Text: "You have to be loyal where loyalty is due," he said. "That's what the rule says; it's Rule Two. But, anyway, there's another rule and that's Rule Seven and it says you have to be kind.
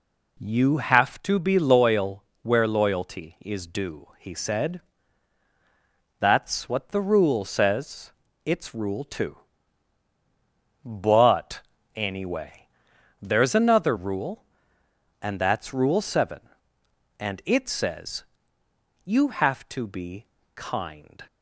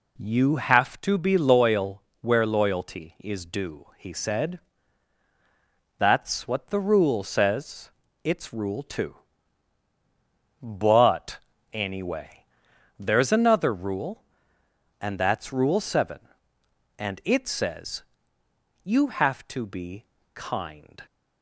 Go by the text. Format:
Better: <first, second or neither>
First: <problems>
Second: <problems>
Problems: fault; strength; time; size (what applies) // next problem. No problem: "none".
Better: neither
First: pauses between "loyal" and "where"; slight; at 2.2 s; 0.20 s long // pauses between "says" and "you"; noticeable; at 18.2 s; 0.82 s long // pauses between "be" and "kind"; slight; at 20.2 s; 0.28 s long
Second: pauses between "loyal" and "where"; slight; at 2.0 s; 0.20 s long // pauses between "says" and "you"; noticeable; at 18.0 s; 0.82 s long // pauses between "be" and "kind"; slight; at 20.0 s; 0.28 s long